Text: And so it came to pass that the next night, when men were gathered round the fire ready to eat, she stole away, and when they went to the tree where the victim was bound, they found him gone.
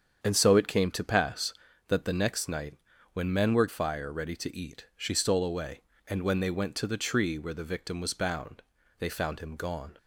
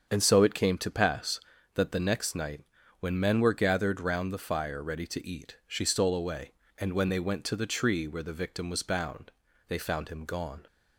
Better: second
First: starts louder than the rest; strong; until 1.2 s; 8 dB // skips "gathered round the"; at 3.6 s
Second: starts louder than the rest; strong; until 1.1 s; 7 dB

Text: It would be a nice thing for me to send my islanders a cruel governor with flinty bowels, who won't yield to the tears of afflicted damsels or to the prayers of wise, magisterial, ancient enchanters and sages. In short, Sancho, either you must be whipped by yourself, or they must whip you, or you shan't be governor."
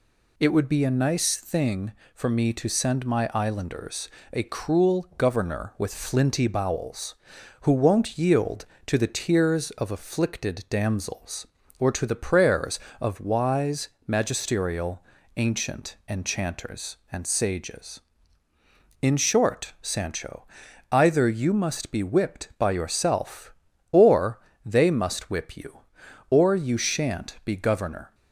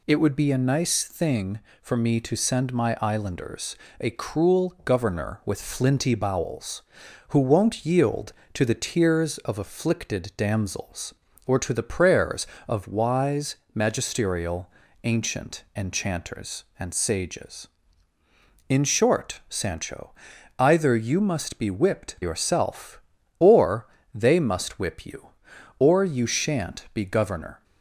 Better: first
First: pauses between "islanders" and "a"; slight; at 4.0 s; 0.24 s long // pauses between "or" and "they"; slight; at 24.3 s; 0.28 s long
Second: pauses between "islanders" and "a"; slight; at 3.7 s; 0.24 s long // skips "by"; at 22.1 s // pauses between "or" and "they"; slight; at 23.8 s; 0.30 s long

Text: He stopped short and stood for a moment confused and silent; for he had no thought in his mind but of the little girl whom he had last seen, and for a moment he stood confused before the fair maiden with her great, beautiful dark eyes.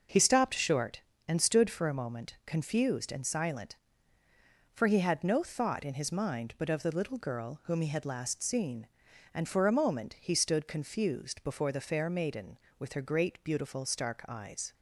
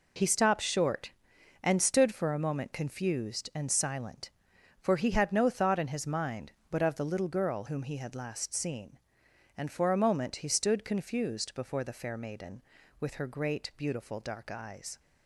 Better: second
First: says "stark" for "dark"; at 13.8 s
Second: none

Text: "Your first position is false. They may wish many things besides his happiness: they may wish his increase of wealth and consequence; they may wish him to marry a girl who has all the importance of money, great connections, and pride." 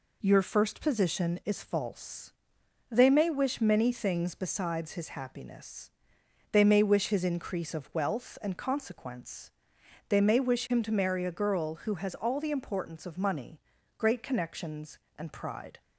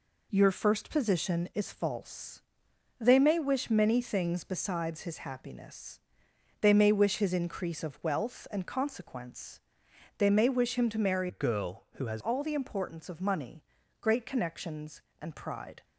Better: first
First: none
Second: changes voice from "a" to "has"; from 11.2 to 12.2 s; 1.0 s long

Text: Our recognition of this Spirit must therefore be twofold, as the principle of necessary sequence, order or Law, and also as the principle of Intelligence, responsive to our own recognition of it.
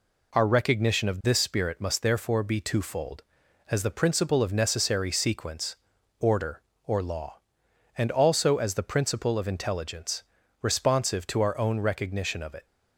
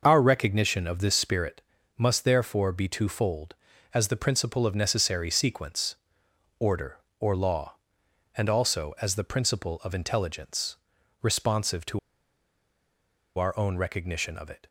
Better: first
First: none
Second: pauses between "Spirit" and "must"; slight; at 1.6 s; 0.34 s long // pauses between "to" and "our"; strong; at 11.9 s; 1.3 s long

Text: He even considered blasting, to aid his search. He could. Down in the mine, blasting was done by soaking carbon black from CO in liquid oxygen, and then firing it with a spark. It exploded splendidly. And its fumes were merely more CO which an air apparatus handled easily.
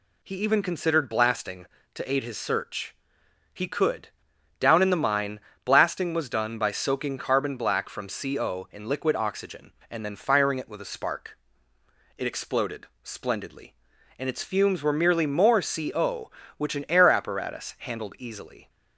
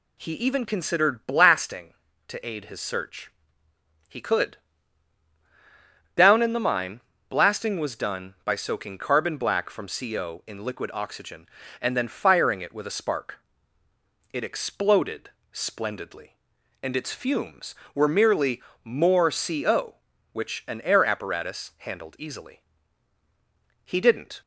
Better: first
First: pauses between "exploded" and "splendidly"; slight; at 12.8 s; 0.16 s long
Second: pauses between "exploded" and "splendidly"; slight; at 15.3 s; 0.22 s long // pauses between "merely" and "more"; slight; at 18.6 s; 0.22 s long // goes on to say "He didn't"; from 23.8 s on; 0.56 s long

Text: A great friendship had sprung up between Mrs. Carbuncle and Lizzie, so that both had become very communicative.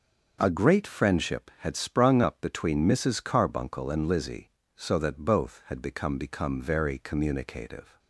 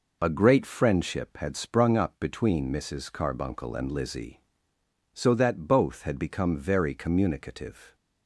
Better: second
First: says "become" twice; at 6.1 s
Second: none

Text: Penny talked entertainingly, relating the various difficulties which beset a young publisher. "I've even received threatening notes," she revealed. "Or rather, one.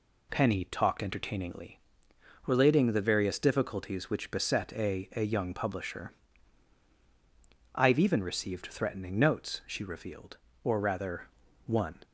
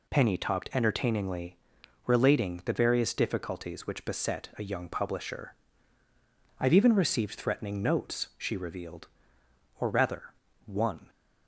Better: second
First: says "a" twice; at 5.1 s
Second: none

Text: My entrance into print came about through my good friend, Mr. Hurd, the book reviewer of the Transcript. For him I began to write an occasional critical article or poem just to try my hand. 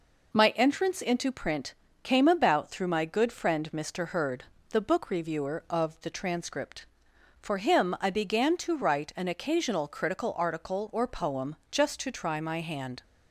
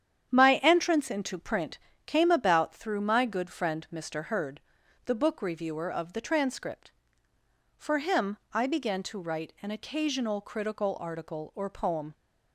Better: first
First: pauses between "print" and "came"; slight; at 1.7 s; 0.30 s long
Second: starts louder than the rest; strong; until 1.3 s; 9 dB // pauses between "print" and "came"; slight; at 1.7 s; 0.26 s long // pauses between "him" and "I"; slight; at 8.3 s; 0.16 s long // stops before "just to try my hand"; at 12.1 s

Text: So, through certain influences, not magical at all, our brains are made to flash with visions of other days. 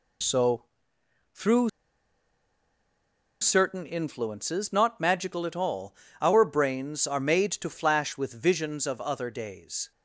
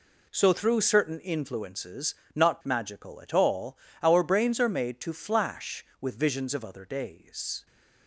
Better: second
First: pauses between "through" and "certain"; strong; at 1.6 s; 1.7 s long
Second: none

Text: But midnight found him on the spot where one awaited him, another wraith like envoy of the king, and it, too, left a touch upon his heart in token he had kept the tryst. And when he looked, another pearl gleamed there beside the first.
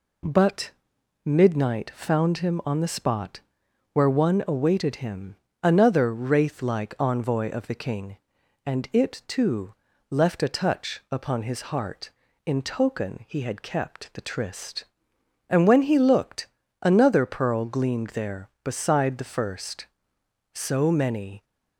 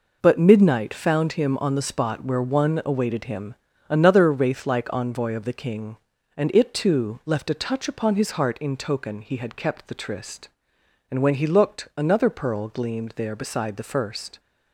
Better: second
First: pauses between "But" and "midnight"; noticeable; at 0.7 s; 0.56 s long // pauses between "spot" and "where"; noticeable; at 3.4 s; 0.52 s long // goes on to say "So many"; noticeable; from 20.5 s on; 0.90 s long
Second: none

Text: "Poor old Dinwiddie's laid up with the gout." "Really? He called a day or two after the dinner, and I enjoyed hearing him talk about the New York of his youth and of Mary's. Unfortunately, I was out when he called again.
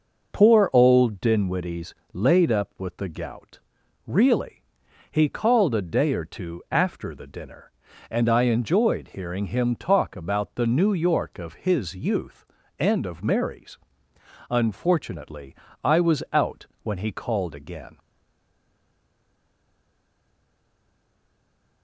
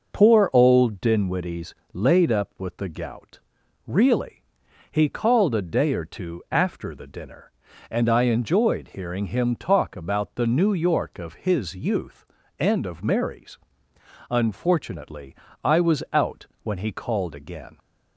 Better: second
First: pauses between "Dinwiddie's" and "laid"; slight; at 1.9 s; 0.22 s long // pauses between "out" and "when"; slight; at 16.6 s; 0.18 s long // stays silent after the last word; strong; from 17.9 s on; 3.9 s long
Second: pauses between "Dinwiddie's" and "laid"; slight; at 1.7 s; 0.22 s long // pauses between "out" and "when"; slight; at 16.4 s; 0.18 s long

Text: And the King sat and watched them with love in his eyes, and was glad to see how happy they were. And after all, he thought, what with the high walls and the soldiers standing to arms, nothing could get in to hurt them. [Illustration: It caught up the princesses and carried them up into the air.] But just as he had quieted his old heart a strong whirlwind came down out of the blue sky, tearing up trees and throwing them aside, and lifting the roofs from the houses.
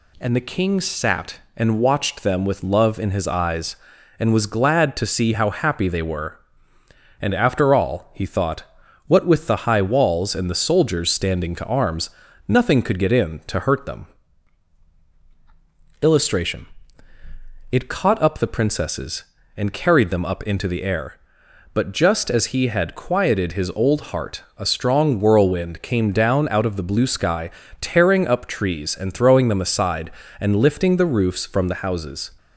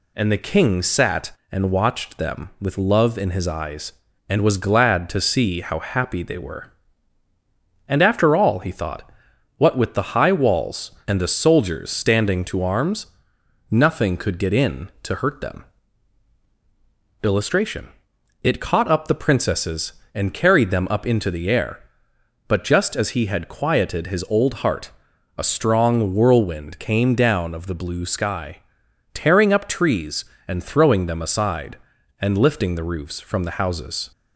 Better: first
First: pauses between "heart" and "a"; slight; at 24.4 s; 0.16 s long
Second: pauses between "heart" and "a"; noticeable; at 24.9 s; 0.46 s long // skips "out"; at 27.5 s

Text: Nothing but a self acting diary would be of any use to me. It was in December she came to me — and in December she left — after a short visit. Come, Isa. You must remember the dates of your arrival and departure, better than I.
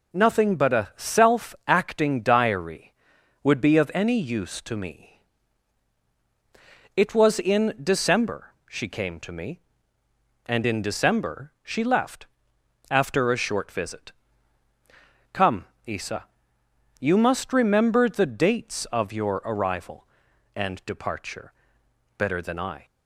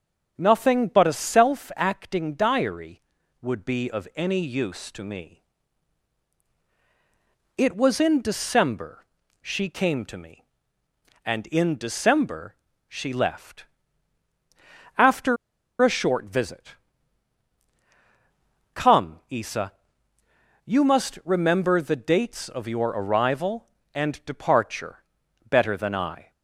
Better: first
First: pauses between "December" and "she"; slight; at 8.5 s; 0.16 s long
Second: pauses between "December" and "she"; slight; at 9.0 s; 0.36 s long // pauses between "December" and "she"; slight; at 12.5 s; 0.34 s long // pauses between "after" and "a"; at 15.3 s; 0.45 s long

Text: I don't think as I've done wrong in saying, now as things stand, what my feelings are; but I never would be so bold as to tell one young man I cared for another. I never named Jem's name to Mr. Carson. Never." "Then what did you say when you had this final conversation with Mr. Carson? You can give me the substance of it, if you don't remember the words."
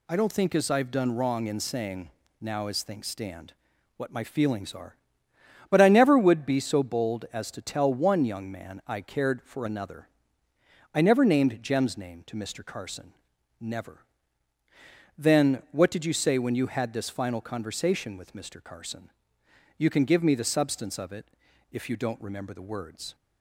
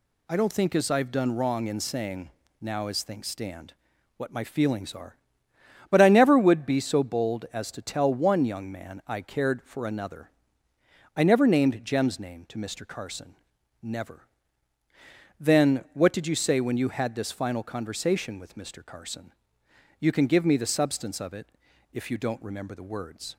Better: neither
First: none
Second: none

